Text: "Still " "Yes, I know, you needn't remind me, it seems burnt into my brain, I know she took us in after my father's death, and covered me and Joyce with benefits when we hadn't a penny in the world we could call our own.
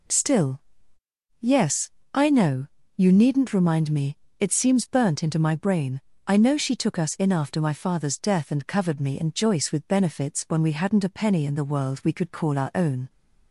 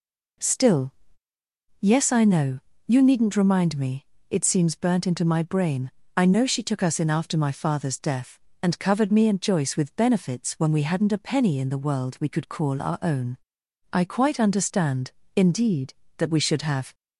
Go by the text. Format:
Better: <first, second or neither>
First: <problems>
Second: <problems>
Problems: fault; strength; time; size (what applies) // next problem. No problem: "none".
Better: first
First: none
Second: goes on to say "I quite understand indeed that we should have"; strong; from 13.9 s on; 3.0 s long